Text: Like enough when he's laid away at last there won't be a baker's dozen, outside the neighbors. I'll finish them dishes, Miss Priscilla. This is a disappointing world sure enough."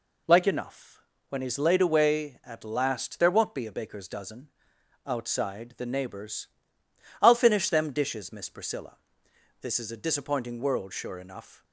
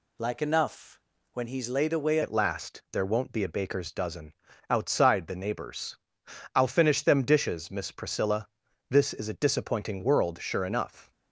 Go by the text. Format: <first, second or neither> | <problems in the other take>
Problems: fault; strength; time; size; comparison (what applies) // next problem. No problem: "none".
first | pauses between "enough" and "when"; slight; at 1.0 s; 0.32 s long; slight in the first // changes voice at "at"; from 2.2 s on; 8.9 s long